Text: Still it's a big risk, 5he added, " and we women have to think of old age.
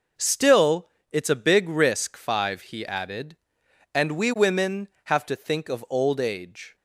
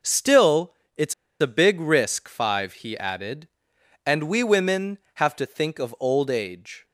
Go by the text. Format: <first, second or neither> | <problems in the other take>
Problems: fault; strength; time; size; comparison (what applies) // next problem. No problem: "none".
first | pauses between "Still" and "it's"; slight; at 0.7 s; 0.22 s long; slight in the first // pauses between "it's" and "a"; slight; at 1.1 s; 0.27 s long